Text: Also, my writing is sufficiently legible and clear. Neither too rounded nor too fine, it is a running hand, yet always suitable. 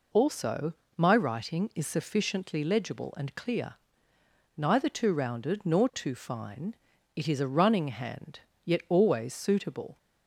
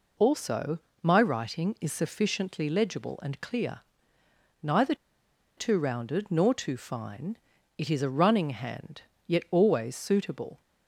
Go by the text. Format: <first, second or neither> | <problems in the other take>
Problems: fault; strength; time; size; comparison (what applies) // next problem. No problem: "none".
first | pauses between "Neither" and "too"; noticeable; at 4.9 s; 0.61 s long